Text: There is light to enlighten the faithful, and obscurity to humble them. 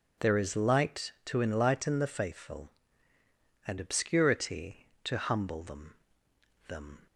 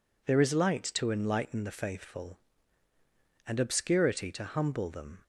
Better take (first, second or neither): second